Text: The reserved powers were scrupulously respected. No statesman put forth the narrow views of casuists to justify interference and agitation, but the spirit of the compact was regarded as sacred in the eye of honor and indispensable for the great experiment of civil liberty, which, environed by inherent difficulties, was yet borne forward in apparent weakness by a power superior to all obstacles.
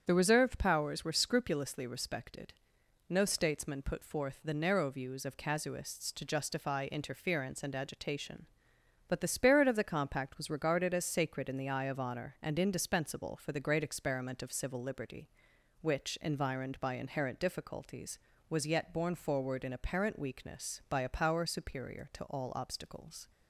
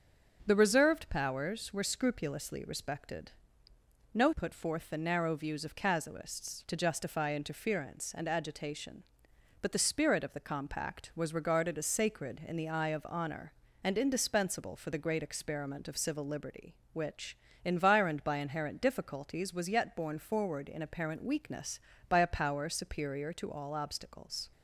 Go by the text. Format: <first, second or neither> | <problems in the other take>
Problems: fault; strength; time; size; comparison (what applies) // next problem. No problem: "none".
first | starts louder than the rest; strong; until 1.4 s; 7.5 dB; strong in the first // skips "statesman"; at 4.3 s